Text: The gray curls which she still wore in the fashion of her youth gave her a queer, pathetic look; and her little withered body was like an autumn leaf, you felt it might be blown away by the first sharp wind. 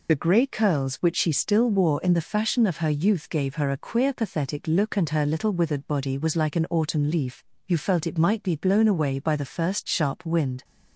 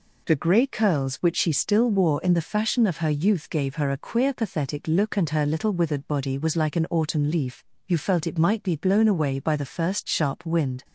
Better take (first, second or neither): second